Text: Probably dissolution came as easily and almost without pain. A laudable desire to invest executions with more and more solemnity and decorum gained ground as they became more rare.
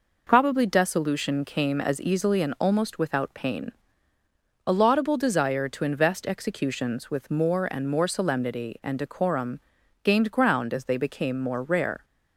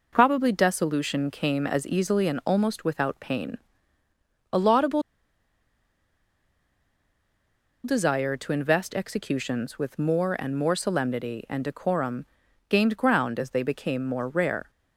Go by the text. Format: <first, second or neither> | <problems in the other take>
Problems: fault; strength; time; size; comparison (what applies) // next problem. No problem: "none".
first | pauses between "laudable" and "desire"; strong; at 5.0 s; 2.8 s long // pauses between "decorum" and "gained"; noticeable; at 12.2 s; 0.46 s long; noticeable in the first